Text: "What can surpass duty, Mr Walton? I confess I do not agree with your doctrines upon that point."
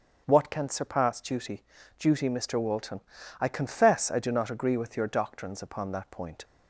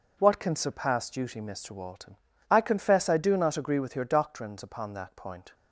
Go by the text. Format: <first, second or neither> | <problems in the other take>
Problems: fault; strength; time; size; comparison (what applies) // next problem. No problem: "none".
second | starts louder than the rest; until 1.2 s; 7 dB // says "duty" twice; at 1.9 s